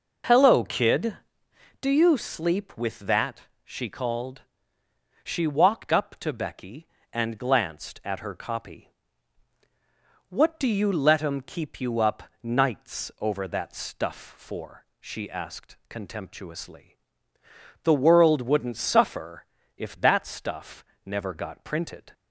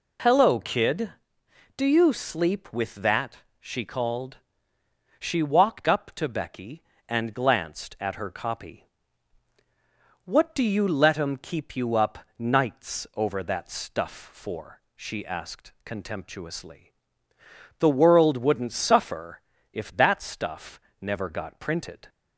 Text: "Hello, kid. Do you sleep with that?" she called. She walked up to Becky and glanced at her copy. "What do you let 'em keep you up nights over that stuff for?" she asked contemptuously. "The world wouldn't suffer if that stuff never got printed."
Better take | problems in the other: second | starts louder than the rest; noticeable; until 1.9 s; 5.5 dB // pauses between "up" and "nights"; slight; at 12.2 s; 0.18 s long; slight in the second // pauses between "suffer" and "if"; slight; at 19.4 s; 0.32 s long; slight in the second // pauses between "stuff" and "never"; slight; at 20.8 s; 0.22 s long; slight in the second

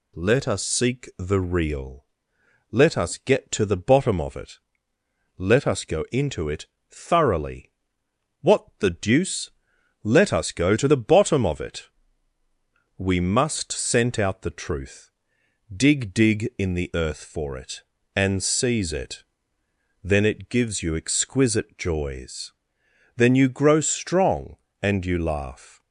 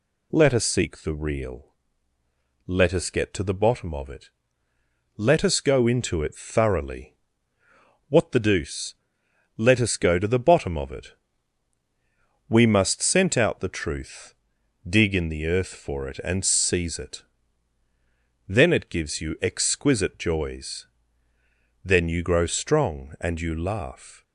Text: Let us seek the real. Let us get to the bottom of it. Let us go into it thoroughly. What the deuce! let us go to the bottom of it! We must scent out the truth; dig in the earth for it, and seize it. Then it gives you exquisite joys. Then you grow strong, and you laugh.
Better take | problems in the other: second | pauses between "it" and "thoroughly"; slight; at 6.6 s; 0.24 s long // says "dig" twice; at 16.1 s

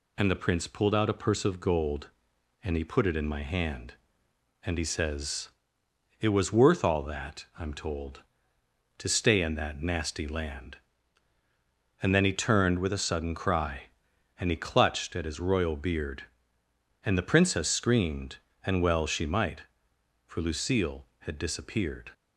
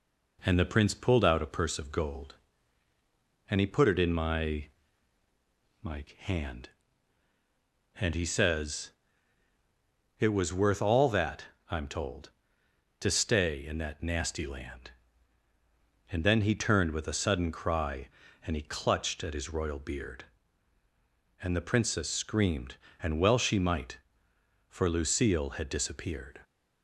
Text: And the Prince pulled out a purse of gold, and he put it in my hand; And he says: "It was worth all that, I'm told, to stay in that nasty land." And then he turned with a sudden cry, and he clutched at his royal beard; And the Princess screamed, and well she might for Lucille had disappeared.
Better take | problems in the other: first | says "my" twice; at 5.8 s

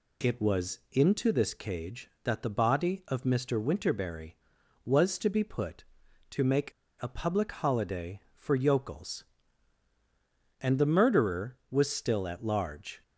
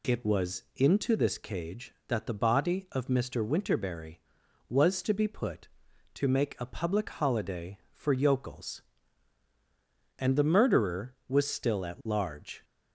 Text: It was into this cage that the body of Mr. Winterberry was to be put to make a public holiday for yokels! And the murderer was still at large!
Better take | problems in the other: second | pauses between "make" and "a"; slight; at 6.6 s; 0.32 s long

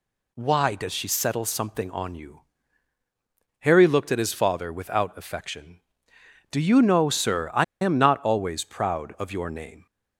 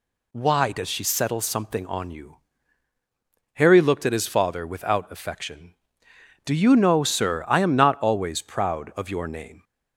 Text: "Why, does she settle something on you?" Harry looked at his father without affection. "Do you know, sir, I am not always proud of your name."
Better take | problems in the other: second | pauses between "I" and "am"; slight; at 7.6 s; 0.19 s long

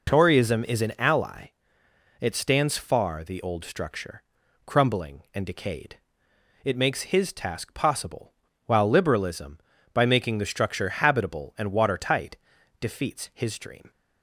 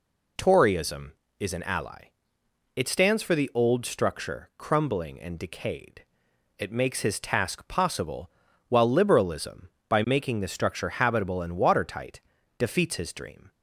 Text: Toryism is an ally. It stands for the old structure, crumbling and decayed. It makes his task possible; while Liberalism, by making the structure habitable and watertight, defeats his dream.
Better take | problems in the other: second | says "far" for "for"; at 2.7 s

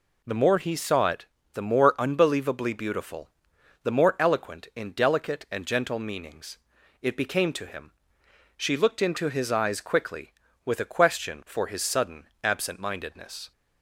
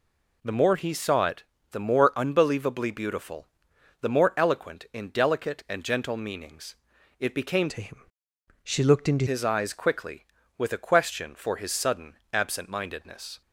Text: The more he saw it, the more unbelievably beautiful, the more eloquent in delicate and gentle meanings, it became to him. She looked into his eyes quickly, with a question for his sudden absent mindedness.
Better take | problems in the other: first | changes voice from "to" to "into"; from 7.6 to 9.2 s; 1.6 s long // pauses between "sudden" and "absent"; slight; at 12.1 s; 0.18 s long; slight in the first

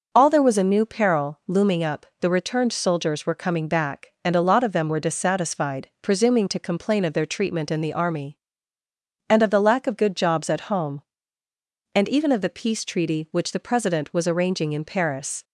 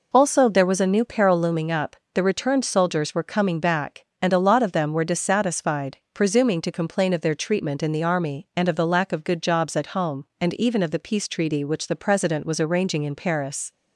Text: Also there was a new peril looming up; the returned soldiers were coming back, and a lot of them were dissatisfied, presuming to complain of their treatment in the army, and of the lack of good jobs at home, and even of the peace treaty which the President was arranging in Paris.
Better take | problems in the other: second | says "All" for "Also"; at 0.1 s

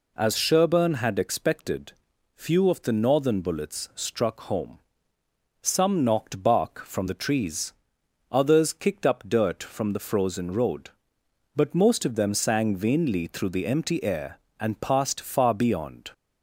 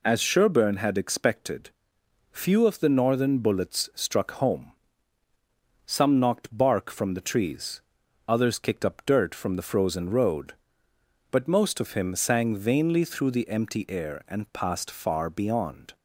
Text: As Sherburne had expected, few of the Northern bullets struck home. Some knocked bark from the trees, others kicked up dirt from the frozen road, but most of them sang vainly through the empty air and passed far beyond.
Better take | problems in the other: first | says "him" for "them"; at 11.9 s

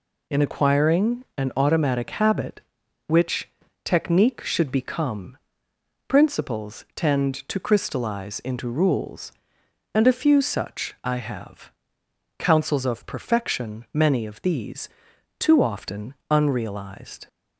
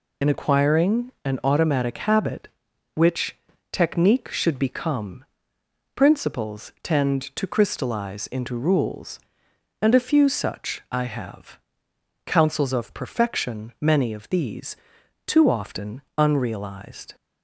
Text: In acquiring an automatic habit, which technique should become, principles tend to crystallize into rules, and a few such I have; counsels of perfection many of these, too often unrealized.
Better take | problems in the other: first | loses the start of "In"; at 0.2 s; 45 ms // pauses between "which" and "technique"; at 3.3 s; 0.38 s long; also in the first // pauses between "often" and "unrealized"; slight; at 16.0 s; 0.16 s long; slight in the first

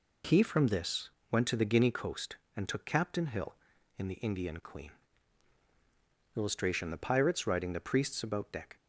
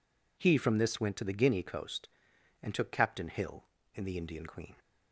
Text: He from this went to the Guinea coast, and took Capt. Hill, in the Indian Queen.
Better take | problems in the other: second | pauses between "this" and "went"; slight; at 1.0 s; 0.20 s long // goes on to say "Illustration The Pirates riding the Priests about deck"; strong; from 6.3 s on; 2.4 s long

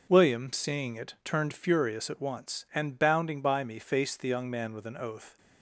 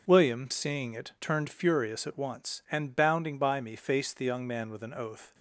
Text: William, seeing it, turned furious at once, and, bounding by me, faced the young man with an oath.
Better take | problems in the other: neither | none

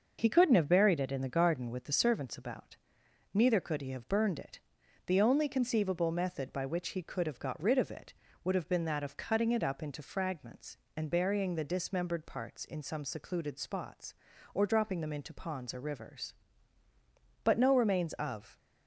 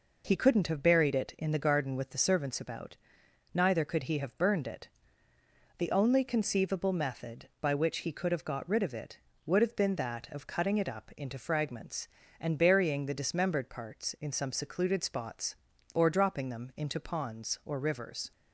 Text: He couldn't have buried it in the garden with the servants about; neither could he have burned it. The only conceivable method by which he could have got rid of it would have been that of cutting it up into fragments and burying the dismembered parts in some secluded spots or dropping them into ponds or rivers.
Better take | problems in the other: second | goes on to say "But no remains of"; noticeable; from 17.4 s on; 1.1 s long

